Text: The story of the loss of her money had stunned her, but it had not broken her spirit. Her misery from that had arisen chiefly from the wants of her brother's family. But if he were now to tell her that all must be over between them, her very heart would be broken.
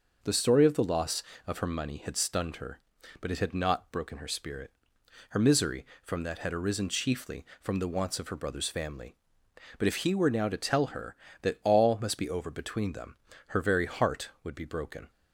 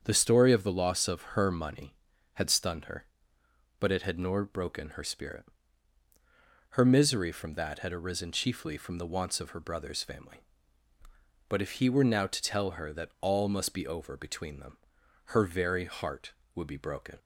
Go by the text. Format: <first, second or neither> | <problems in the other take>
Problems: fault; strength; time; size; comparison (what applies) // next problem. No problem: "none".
first | starts louder than the rest; strong; until 1.0 s; 7.5 dB // says "nor" for "not"; at 4.1 s